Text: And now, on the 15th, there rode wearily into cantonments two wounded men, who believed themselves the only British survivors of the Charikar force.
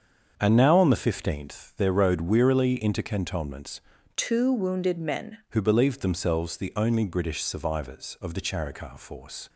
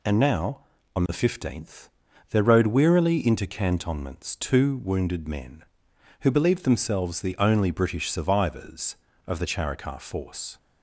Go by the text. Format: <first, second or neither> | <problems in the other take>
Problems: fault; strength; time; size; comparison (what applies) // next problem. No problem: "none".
second | starts louder than the rest; until 1.3 s; 7 dB // changes voice from "two" to "men"; from 4.1 to 5.3 s; 1.2 s long